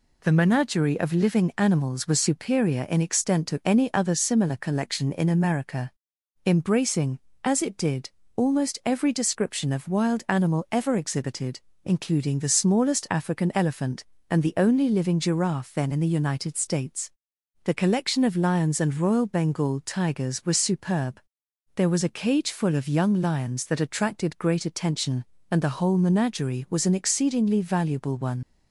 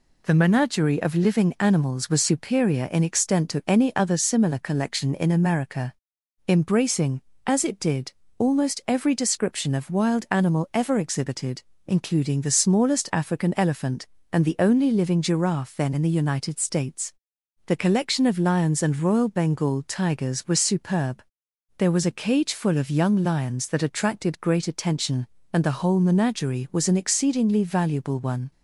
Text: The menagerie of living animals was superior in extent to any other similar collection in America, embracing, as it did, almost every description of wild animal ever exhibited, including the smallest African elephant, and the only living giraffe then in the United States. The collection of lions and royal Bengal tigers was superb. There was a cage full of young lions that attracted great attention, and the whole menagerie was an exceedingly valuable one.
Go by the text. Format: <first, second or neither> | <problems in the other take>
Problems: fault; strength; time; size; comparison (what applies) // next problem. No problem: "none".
second | leaves "one" unfinished; at 28.4 s; 50 ms